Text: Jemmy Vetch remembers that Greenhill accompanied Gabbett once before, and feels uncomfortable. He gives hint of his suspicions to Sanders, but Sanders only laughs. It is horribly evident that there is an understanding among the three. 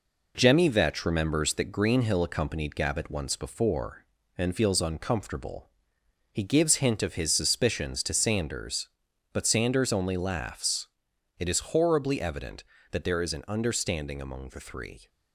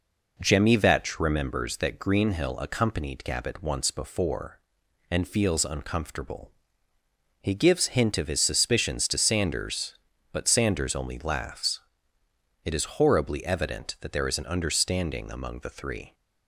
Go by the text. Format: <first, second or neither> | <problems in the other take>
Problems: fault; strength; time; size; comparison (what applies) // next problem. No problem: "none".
second | gets quieter; noticeable; throughout; 4.5 dB